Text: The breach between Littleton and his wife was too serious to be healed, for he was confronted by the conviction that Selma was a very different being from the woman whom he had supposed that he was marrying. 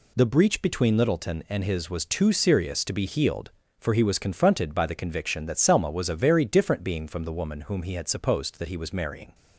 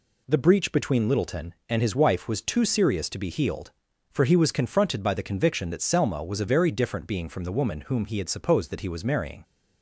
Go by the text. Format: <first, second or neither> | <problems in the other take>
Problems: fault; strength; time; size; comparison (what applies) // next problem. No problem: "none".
second | skips "wife"; at 1.8 s